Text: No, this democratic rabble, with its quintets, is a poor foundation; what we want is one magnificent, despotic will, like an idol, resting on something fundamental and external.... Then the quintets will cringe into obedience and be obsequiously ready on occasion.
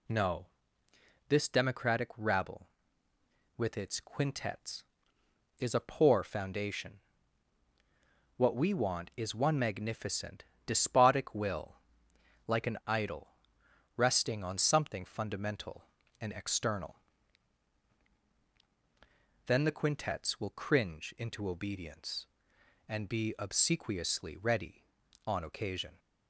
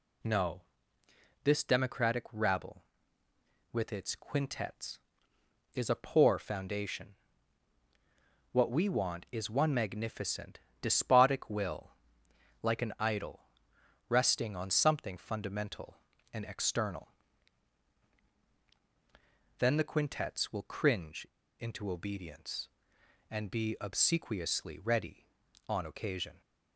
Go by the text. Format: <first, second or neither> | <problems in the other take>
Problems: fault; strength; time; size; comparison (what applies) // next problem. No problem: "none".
first | pauses between "cringe" and "into"; slight; at 21.2 s; 0.31 s long